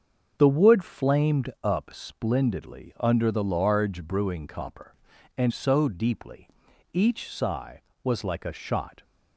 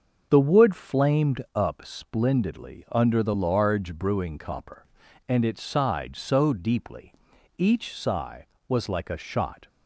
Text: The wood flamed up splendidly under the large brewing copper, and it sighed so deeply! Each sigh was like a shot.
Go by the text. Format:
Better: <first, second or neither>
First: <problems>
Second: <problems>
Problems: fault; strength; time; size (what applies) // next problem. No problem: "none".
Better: second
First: starts louder than the rest; until 1.3 s; 7 dB // skips "it sighed"; at 5.5 s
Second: starts louder than the rest; until 1.3 s; 6.5 dB